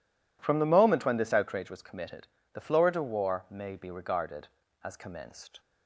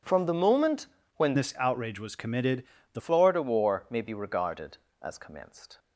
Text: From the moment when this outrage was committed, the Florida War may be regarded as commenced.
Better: first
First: none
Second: pauses between "moment" and "when"; slight; at 0.8 s; 0.30 s long // changes voice from "this" to "the"; from 1.3 to 3.0 s; 1.7 s long

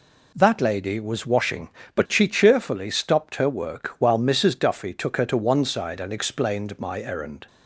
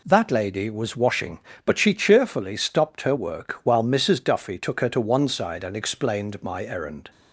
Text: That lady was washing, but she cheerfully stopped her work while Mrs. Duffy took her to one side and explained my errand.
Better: neither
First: none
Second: none

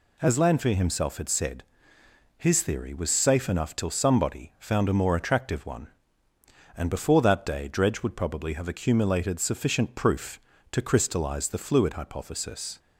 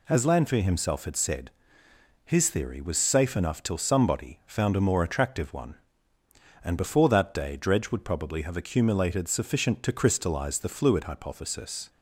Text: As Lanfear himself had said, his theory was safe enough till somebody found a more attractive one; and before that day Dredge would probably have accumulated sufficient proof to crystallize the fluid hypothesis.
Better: first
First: none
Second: skips "proof"; at 9.8 s

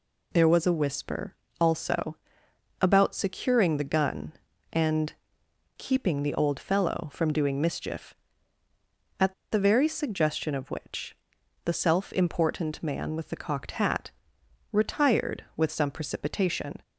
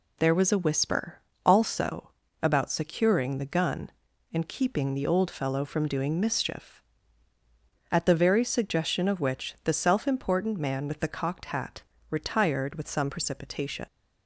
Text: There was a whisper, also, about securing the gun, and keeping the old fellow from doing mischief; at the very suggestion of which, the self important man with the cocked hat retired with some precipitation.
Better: second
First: pauses between "and" and "keeping"; noticeable; at 5.1 s; 0.64 s long // pauses between "at" and "the"; slight; at 9.3 s; 0.18 s long // pauses between "hat" and "retired"; noticeable; at 14.1 s; 0.58 s long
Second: pauses between "hat" and "retired"; slight; at 11.8 s; 0.30 s long

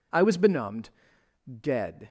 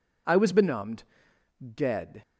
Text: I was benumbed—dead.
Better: neither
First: none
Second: none

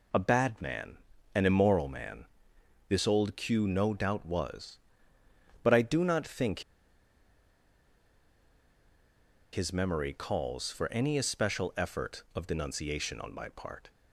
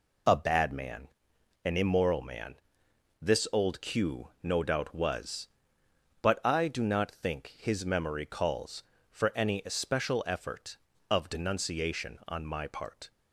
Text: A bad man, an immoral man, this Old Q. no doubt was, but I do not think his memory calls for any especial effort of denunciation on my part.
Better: second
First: pauses between "think" and "his"; strong; at 6.6 s; 2.9 s long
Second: none

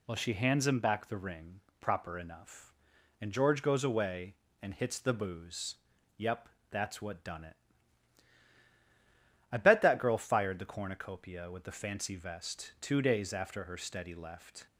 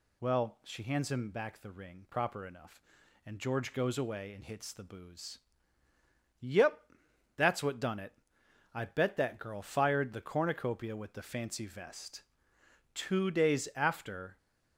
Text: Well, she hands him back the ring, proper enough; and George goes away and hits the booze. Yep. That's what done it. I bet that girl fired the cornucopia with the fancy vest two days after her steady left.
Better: first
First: none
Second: pauses between "vest" and "two"; noticeable; at 12.2 s; 0.70 s long // stops before "her steady left"; at 14.3 s

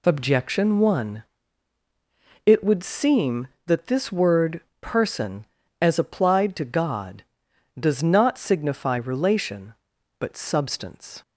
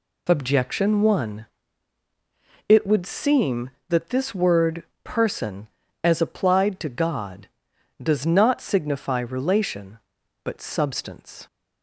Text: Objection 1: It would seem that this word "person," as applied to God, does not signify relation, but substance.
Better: neither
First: pauses between "word" and "person"; slight; at 4.6 s; 0.18 s long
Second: pauses between "word" and "person"; slight; at 4.8 s; 0.18 s long

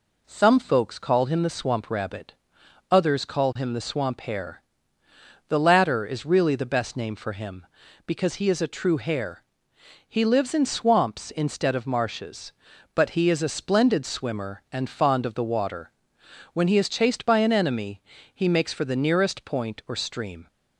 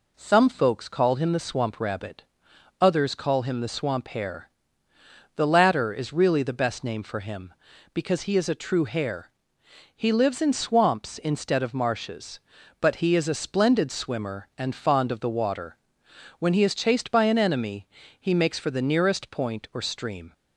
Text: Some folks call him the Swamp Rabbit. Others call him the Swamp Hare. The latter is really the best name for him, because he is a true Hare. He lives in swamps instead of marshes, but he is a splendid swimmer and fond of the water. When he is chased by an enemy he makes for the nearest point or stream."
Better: neither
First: pauses between "enemy" and "he"; slight; at 18.0 s; 0.32 s long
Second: pauses between "enemy" and "he"; slight; at 17.8 s; 0.32 s long

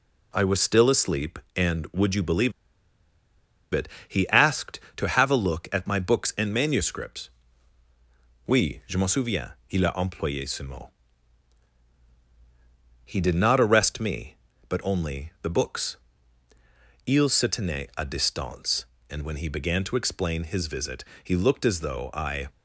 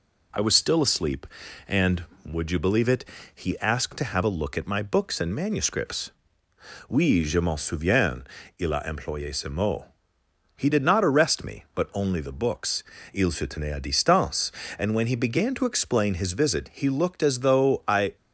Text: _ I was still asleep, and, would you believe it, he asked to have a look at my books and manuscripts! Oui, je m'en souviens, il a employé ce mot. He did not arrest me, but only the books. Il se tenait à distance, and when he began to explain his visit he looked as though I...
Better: second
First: pauses between "believe" and "it"; at 2.5 s; 1.2 s long // pauses between "visit" and "he"; slight; at 21.0 s; 0.18 s long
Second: none

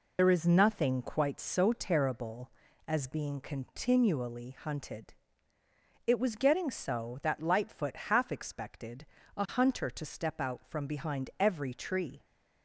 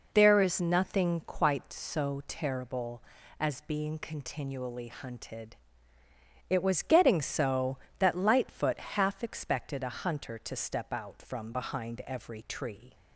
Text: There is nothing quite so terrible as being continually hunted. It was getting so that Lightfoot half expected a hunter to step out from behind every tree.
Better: second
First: loses the start of "There"; at 0.1 s; 55 ms // pauses between "expected" and "a"; slight; at 9.0 s; 0.30 s long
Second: none

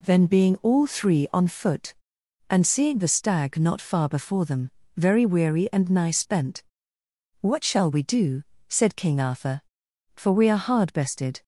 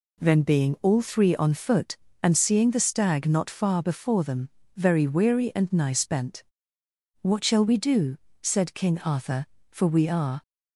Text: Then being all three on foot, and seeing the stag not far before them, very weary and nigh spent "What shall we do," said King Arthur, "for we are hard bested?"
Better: first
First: pauses between "spent" and "What"; noticeable; at 6.6 s; 0.78 s long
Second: pauses between "spent" and "What"; noticeable; at 6.4 s; 0.80 s long // stops before "hard bested"; at 10.4 s

